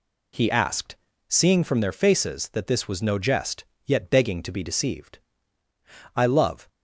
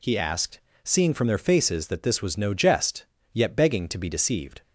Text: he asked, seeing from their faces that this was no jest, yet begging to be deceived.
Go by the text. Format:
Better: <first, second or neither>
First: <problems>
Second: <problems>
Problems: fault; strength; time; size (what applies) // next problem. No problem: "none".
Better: second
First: goes on to say "I love"; from 6.1 s on; 0.50 s long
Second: none